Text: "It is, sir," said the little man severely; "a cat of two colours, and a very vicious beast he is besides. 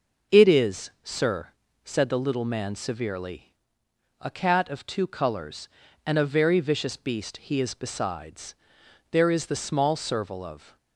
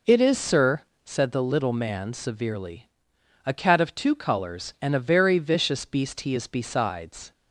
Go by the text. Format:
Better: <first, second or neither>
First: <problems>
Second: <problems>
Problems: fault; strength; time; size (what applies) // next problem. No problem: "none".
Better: second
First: goes on to say "There is the small serval of"; strong; from 9.1 s on; 1.6 s long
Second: none